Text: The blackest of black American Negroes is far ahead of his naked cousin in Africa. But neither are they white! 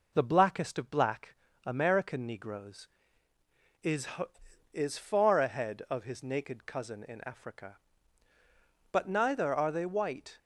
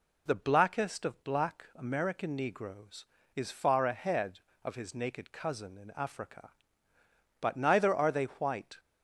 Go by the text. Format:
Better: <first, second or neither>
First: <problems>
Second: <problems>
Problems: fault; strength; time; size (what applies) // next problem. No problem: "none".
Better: second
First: pauses between "black" and "American"; slight; at 1.3 s; 0.29 s long // says "is" twice; at 4.7 s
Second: none